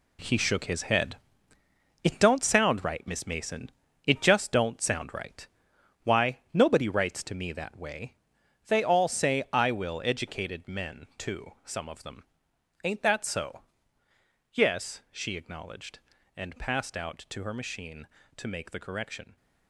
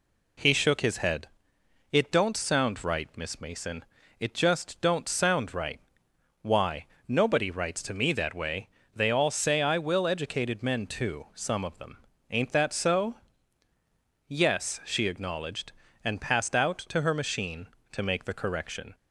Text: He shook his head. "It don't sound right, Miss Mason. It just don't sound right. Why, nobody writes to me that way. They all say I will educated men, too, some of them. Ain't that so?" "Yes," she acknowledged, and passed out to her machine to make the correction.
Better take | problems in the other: second | gets quieter; strong; throughout; 9.5 dB

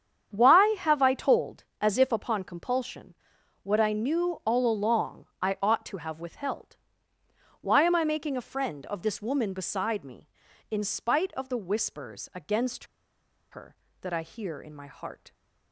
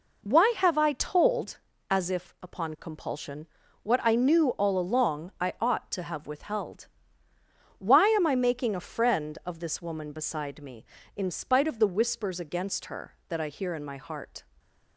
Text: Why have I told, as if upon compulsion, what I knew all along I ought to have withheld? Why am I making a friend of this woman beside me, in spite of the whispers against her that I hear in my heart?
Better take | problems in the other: second | starts louder than the rest; strong; until 1.3 s; 8 dB // pauses between "along" and "I"; slight; at 5.2 s; 0.16 s long // pauses between "against" and "her"; noticeable; at 12.8 s; 0.65 s long

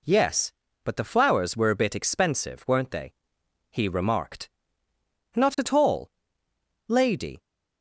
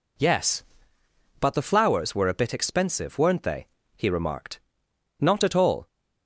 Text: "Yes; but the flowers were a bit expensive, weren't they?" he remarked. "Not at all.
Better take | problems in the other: second | goes on to say "Lady"; from 6.8 s on; 0.54 s long

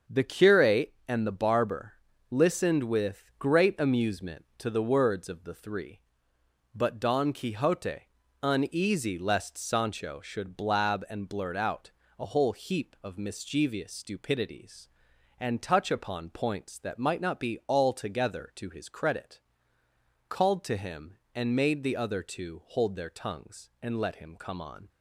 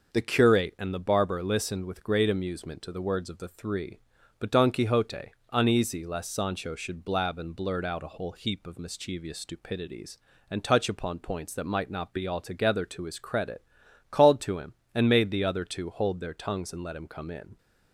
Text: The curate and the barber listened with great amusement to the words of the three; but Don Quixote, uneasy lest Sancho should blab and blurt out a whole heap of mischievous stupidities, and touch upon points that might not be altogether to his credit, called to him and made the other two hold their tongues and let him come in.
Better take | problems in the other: second | starts louder than the rest; until 1.2 s; 6.5 dB // pauses between "barber" and "listened"; slight; at 1.9 s; 0.36 s long // pauses between "out" and "a"; slight; at 11.9 s; 0.30 s long // says "on" for "in"; at 24.6 s

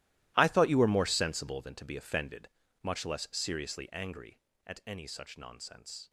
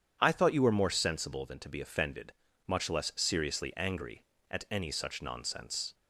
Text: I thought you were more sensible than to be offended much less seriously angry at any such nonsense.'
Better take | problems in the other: second | gets quieter; strong; throughout; 16.5 dB // starts louder than the rest; strong; until 1.3 s; 16.5 dB; strong in the second // pauses between "offended" and "much"; slight; at 2.4 s; 0.34 s long; slight in the second

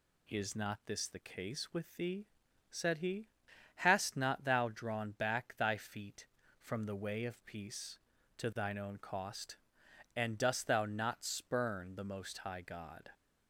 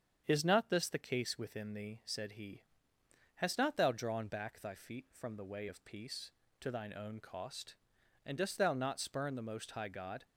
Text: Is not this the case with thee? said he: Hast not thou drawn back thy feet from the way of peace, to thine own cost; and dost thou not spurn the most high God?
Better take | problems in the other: first | starts louder than the rest; strong; until 1.2 s; 7.5 dB // says "within" for "with"; at 1.3 s

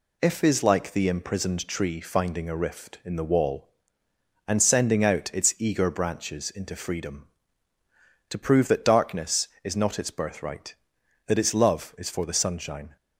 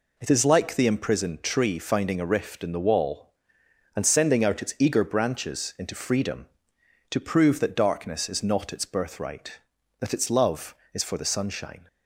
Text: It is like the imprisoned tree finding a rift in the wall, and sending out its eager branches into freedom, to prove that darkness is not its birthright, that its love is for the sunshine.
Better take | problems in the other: second | says "If" for "It"; at 0.2 s

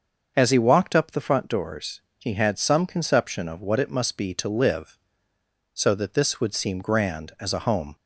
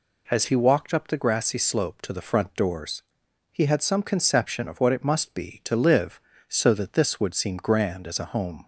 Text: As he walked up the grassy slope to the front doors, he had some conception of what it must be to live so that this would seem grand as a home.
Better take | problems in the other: second | starts louder than the rest; until 1.3 s; 6.5 dB // skips "the grassy slope to"; at 1.1 s

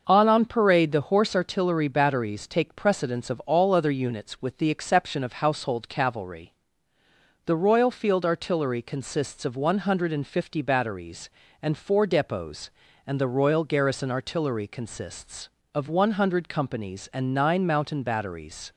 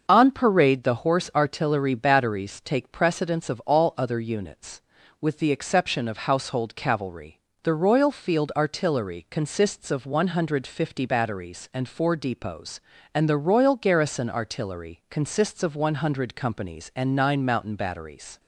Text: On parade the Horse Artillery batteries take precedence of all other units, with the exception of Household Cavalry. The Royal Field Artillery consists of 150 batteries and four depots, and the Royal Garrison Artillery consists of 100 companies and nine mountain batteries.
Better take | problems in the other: second | starts louder than the rest; noticeable; until 1.0 s; 6 dB; also in the second // says "On" twice; at 0.2 s

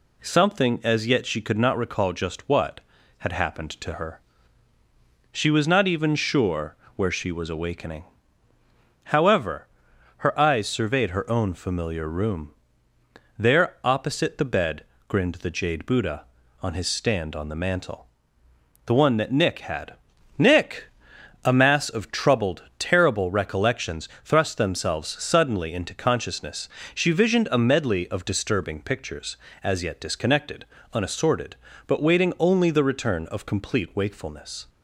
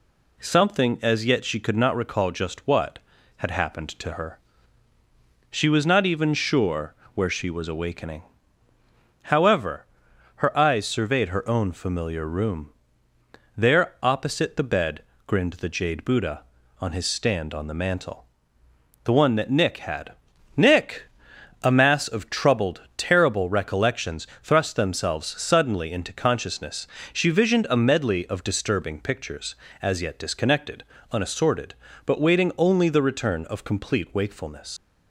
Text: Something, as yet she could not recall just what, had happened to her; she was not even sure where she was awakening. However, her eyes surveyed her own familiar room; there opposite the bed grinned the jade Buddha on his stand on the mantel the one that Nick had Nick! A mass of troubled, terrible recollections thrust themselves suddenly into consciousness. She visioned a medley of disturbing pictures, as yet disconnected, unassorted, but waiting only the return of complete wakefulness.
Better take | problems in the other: first | pauses between "sure" and "where"; slight; at 6.9 s; 0.22 s long; slight in the first // pauses between "bed" and "grinned"; slight; at 15.0 s; 0.24 s long; slight in the first // pauses between "mantel" and "the"; noticeable; at 18.2 s; 0.80 s long; noticeable in the first // pauses between "had" and "Nick"; at 20.1 s; 0.44 s long; also in the first // pauses between "recollections" and "thrust"; slight; at 24.2 s; 0.16 s long; slight in the first // leaves "wakefulness" unfinished; at 34.7 s; 110 ms

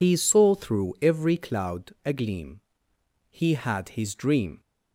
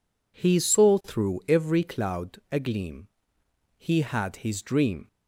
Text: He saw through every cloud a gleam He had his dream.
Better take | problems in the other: second | loses the start of "He"; at 0.0 s; 80 ms // pauses between "gleam" and "He"; noticeable; at 2.5 s; 0.68 s long; noticeable in the second

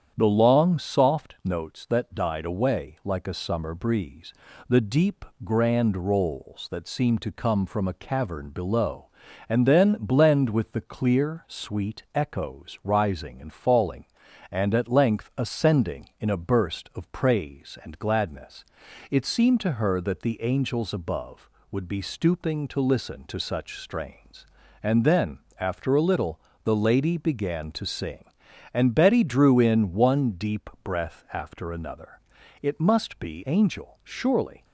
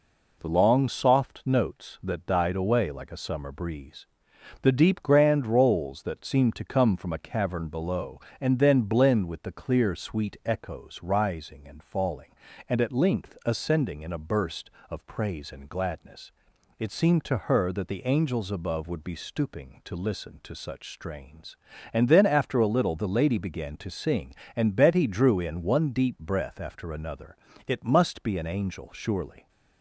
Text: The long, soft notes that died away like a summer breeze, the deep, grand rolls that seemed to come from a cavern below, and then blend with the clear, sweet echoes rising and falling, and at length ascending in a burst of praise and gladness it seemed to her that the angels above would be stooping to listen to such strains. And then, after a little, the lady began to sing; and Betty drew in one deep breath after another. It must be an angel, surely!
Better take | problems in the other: second | starts louder than the rest; strong; until 1.1 s; 8.5 dB // pauses between "gladness" and "it"; noticeable; at 18.6 s; 0.46 s long; noticeable in the second // skips "an"; at 33.4 s

